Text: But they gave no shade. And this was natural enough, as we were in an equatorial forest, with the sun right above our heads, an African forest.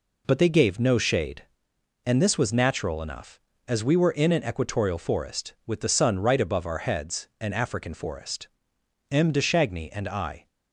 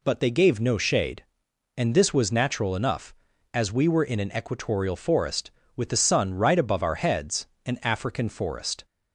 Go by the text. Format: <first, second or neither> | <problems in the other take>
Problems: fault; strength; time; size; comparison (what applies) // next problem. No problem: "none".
second | goes on to say "M de Chagny and I"; from 9.1 s on; 1.3 s long